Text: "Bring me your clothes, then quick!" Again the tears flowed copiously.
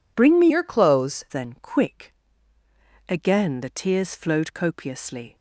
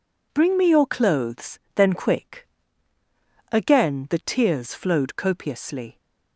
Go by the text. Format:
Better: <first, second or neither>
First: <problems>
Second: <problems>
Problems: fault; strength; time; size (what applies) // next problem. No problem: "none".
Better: second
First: changes voice from "your" to "clothes"; from 0.4 to 1.2 s; 0.8 s long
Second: none